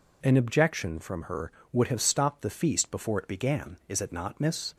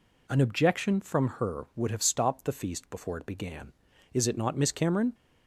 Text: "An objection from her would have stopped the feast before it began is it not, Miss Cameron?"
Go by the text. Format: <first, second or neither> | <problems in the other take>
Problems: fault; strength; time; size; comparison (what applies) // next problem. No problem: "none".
second | stops before "Cameron"; at 4.7 s